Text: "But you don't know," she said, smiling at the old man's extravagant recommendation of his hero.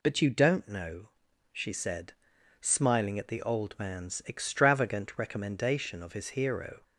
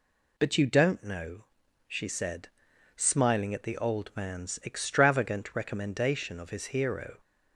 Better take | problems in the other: neither | none

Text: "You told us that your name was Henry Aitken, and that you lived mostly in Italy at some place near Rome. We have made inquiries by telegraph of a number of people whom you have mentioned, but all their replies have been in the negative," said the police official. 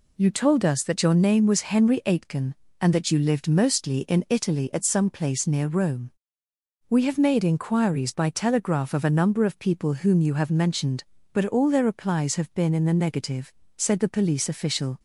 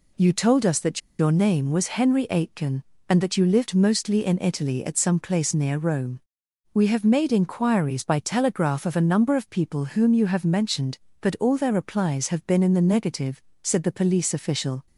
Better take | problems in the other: first | pauses between "that" and "your"; slight; at 0.9 s; 0.19 s long

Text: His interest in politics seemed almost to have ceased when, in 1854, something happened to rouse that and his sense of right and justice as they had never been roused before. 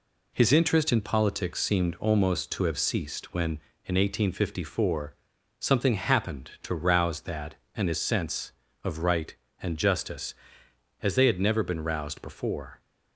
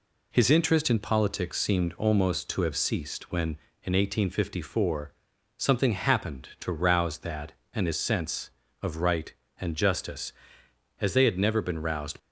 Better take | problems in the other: first | stops before "before"; at 12.1 s

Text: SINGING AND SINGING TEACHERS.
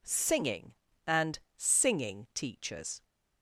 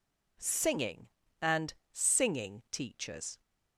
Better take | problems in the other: neither | pauses between "AND" and "SINGING"; slight; the same in both

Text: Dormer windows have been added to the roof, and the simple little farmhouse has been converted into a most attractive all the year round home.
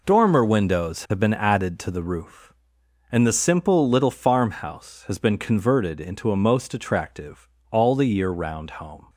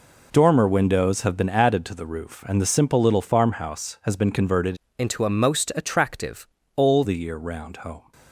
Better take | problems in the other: first | changes voice from "into" to "all"; from 4.9 to 7.0 s; 2.1 s long // pauses between "attractive" and "all"; slight; at 6.4 s; 0.30 s long; slight in the first

